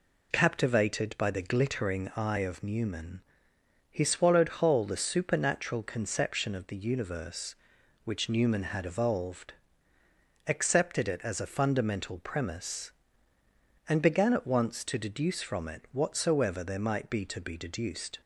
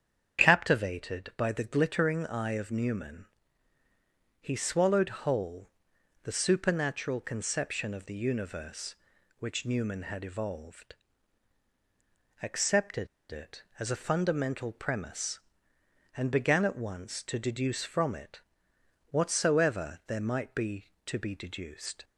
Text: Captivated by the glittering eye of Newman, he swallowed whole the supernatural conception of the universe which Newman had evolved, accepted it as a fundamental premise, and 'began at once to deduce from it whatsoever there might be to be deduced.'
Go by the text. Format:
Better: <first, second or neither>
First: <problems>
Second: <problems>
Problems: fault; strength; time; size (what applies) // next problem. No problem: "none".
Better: first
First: none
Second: starts louder than the rest; strong; until 1.4 s; 8 dB // pauses between "whole" and "the"; noticeable; at 5.6 s; 0.56 s long // pauses between "accepted" and "it"; slight; at 13.0 s; 0.24 s long // pauses between "it" and "whatsoever"; noticeable; at 18.3 s; 0.68 s long